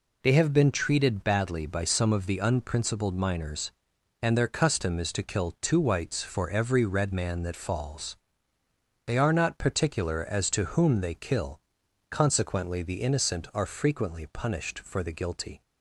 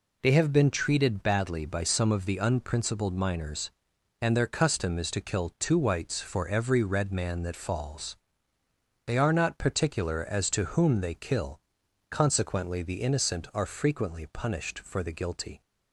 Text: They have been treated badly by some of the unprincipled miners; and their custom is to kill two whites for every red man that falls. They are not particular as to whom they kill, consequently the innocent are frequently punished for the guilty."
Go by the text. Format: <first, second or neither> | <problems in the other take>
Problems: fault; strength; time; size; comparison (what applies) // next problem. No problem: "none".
neither | none